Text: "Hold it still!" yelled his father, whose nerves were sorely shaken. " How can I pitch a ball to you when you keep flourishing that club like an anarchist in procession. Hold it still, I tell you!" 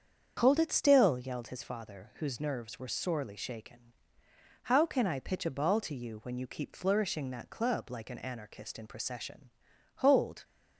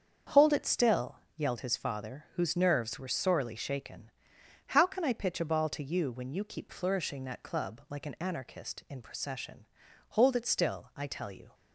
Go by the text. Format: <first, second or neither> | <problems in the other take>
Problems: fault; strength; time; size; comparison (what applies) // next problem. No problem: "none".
second | starts louder than the rest; strong; until 1.3 s; 7.5 dB; also in the second // stops before "it still I tell you"; at 10.4 s